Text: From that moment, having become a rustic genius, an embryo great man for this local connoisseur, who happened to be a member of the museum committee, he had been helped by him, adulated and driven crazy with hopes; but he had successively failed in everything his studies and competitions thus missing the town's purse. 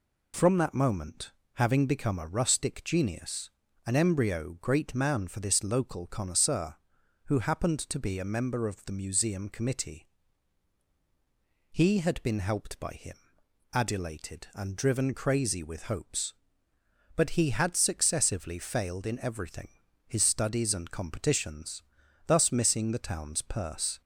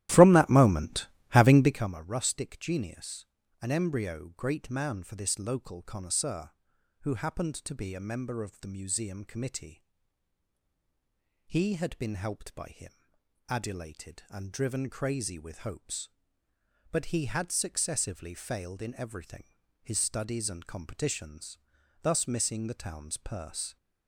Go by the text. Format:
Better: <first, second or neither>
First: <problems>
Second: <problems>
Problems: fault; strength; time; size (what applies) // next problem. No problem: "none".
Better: first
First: pauses between "everything" and "his"; slight; at 19.6 s; 0.36 s long // pauses between "competitions" and "thus"; noticeable; at 21.8 s; 0.46 s long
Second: starts louder than the rest; strong; until 1.9 s; 14 dB // pauses between "everything" and "his"; slight; at 19.4 s; 0.36 s long // pauses between "competitions" and "thus"; noticeable; at 21.5 s; 0.46 s long